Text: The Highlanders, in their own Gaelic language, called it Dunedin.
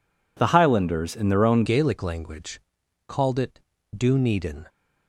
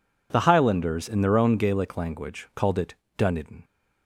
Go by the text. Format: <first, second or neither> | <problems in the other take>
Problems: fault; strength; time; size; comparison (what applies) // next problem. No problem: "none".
second | changes voice at "Gaelic"; from 1.6 s on; 3.0 s long // pauses between "it" and "Dunedin"; slight; at 3.6 s; 0.36 s long; slight in the second